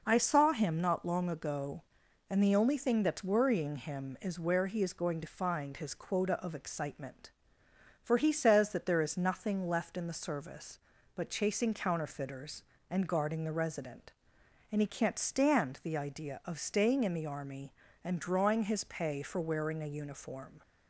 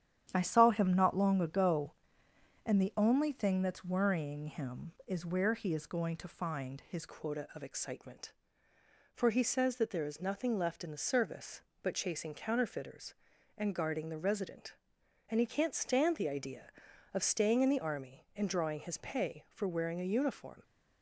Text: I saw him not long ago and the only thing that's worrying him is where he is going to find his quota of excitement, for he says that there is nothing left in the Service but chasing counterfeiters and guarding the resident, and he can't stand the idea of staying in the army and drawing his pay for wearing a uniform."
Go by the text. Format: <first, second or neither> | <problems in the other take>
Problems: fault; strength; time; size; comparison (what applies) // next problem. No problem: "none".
first | starts louder than the rest; strong; until 1.3 s; 10 dB // changes voice at "quota"; from 7.0 s on; 13.6 s long